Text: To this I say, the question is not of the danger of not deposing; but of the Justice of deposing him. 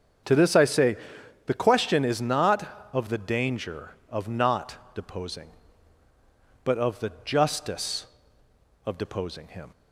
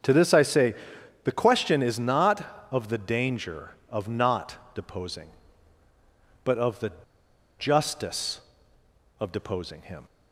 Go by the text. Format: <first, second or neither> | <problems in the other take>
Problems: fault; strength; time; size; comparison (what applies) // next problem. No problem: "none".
first | starts louder than the rest; strong; until 1.5 s; 8 dB; strong in the first // pauses between "the" and "Justice"; noticeable; at 6.9 s; 0.68 s long